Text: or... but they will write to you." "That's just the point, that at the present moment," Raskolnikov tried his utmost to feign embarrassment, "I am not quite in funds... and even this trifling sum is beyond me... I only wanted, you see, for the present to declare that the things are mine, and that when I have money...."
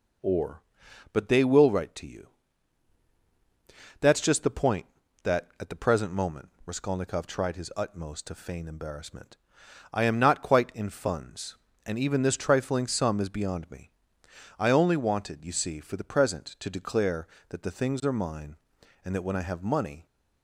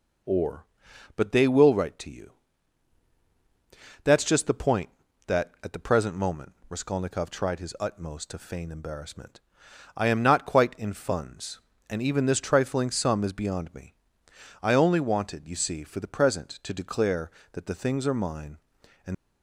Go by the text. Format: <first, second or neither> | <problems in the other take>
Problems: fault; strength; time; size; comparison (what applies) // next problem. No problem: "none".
first | stops before "that when I have money"; at 19.1 s